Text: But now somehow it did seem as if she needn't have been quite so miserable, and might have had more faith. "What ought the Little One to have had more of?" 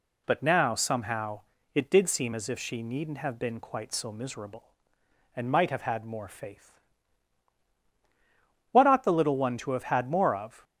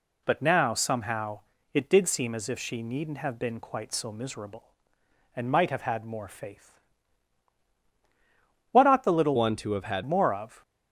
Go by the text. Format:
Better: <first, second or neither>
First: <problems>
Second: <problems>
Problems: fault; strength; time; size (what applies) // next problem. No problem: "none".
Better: first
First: pauses between "somehow" and "it"; slight; at 1.4 s; 0.32 s long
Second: pauses between "somehow" and "it"; slight; at 1.4 s; 0.32 s long // changes voice from "One" to "had"; from 9.3 to 10.0 s; 0.7 s long